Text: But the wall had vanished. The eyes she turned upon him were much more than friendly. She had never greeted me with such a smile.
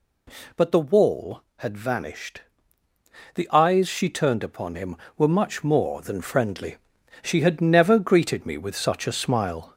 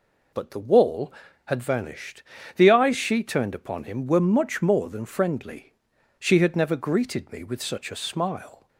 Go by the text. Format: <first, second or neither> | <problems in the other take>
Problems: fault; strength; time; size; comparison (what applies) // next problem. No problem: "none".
second | gets louder; slight; throughout; 2.5 dB